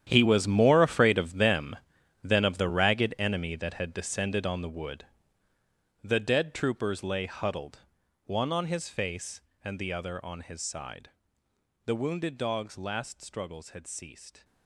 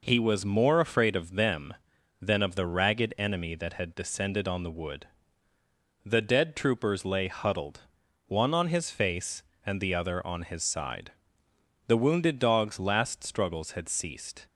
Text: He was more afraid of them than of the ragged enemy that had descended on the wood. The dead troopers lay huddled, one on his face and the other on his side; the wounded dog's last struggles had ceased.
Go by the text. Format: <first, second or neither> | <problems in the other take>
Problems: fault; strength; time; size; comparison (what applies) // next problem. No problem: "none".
second | gets quieter; strong; throughout; 15 dB